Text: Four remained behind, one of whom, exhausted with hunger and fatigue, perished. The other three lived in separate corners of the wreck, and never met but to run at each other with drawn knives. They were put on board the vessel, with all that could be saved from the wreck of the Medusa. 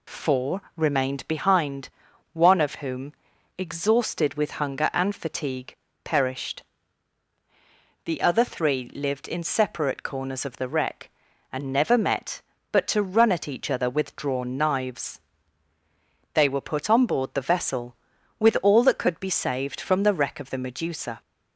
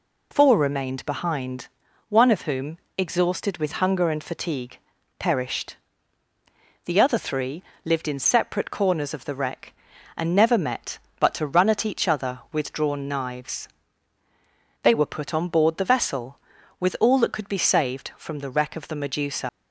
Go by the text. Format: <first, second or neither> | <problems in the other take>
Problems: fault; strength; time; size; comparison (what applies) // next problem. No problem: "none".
first | pauses between "three" and "lived"; slight; at 7.6 s; 0.22 s long // leaves "Medusa" unfinished; at 19.4 s; 110 ms